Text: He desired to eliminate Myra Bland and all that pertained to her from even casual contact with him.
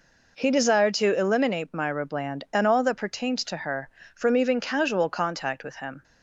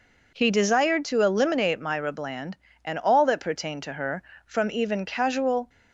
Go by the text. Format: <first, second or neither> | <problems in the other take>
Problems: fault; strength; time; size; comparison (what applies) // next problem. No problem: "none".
first | stops before "contact with him"; at 5.6 s